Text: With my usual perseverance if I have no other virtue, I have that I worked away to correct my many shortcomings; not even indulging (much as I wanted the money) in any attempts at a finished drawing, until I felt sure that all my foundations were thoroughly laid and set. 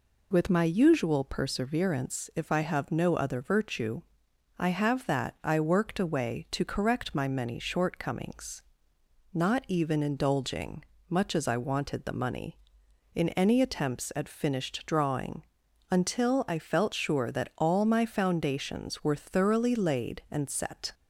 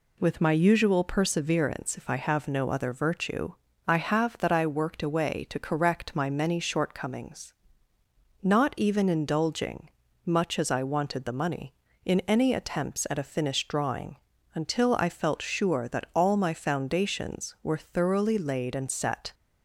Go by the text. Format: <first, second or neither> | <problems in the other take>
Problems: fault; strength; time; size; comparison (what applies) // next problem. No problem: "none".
second | skips "a"; at 14.2 s